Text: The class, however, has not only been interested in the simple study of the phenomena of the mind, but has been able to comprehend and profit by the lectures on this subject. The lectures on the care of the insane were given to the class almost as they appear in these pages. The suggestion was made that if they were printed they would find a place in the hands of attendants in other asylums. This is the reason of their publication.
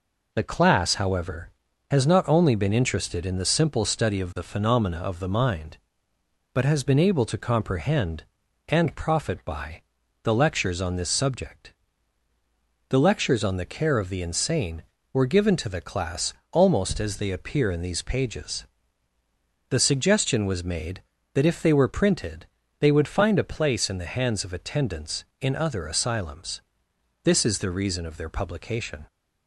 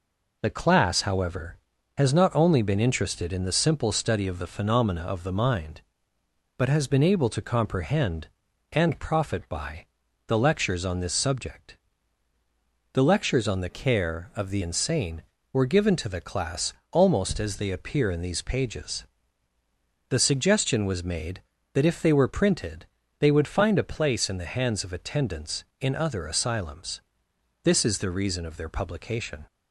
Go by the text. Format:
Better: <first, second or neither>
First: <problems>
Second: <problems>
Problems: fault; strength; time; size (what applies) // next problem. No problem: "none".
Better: first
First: pauses between "by" and "the"; at 9.8 s; 0.42 s long // pauses between "class" and "almost"; slight; at 16.3 s; 0.18 s long // pauses between "printed" and "they"; slight; at 22.4 s; 0.34 s long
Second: pauses between "by" and "the"; at 9.8 s; 0.42 s long // changes voice from "care" to "the"; from 13.6 to 14.6 s; 1.0 s long // pauses between "class" and "almost"; slight; at 16.7 s; 0.18 s long // pauses between "printed" and "they"; slight; at 22.8 s; 0.34 s long